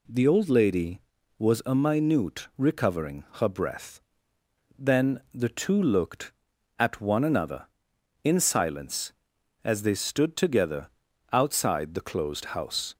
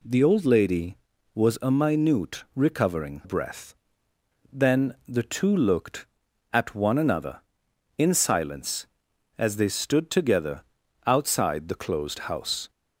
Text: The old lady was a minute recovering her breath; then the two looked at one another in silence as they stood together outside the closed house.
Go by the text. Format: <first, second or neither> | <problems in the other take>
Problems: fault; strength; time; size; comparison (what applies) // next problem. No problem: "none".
first | skips "her"; at 3.2 s // pauses between "together" and "outside"; at 10.6 s; 0.42 s long; also in the first